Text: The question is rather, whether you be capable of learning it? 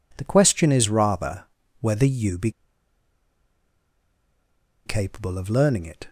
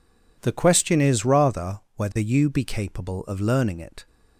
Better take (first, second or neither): second